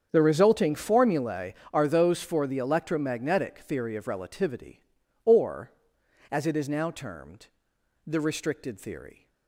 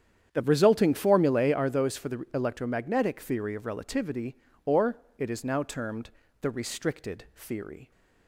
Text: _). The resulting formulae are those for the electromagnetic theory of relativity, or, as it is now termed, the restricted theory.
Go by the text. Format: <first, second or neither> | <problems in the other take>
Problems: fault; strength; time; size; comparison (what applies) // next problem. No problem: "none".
first | starts louder than the rest; strong; until 1.3 s; 9 dB; strong in the first // skips "as"; at 5.0 s